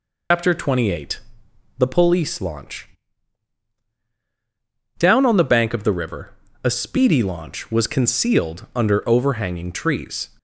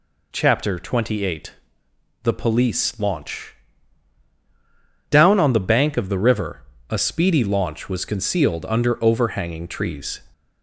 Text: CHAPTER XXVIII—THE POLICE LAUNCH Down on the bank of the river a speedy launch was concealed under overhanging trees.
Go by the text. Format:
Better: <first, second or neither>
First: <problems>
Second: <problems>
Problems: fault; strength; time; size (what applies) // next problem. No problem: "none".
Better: second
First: loses the start of "CHAPTER"; at 0.3 s; 110 ms // pauses between "LAUNCH" and "Down"; strong; at 2.8 s; 2.1 s long // pauses between "river" and "a"; slight; at 6.3 s; 0.32 s long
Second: pauses between "LAUNCH" and "Down"; strong; at 3.5 s; 1.5 s long // pauses between "river" and "a"; slight; at 6.6 s; 0.28 s long